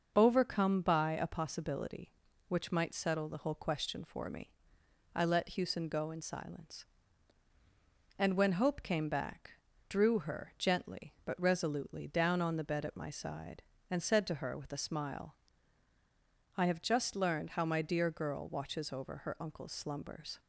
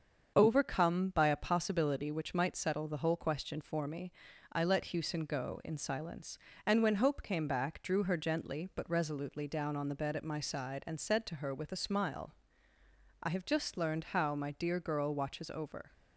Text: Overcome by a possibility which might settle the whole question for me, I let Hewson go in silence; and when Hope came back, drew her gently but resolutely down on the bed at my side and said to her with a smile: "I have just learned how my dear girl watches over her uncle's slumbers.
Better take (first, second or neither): first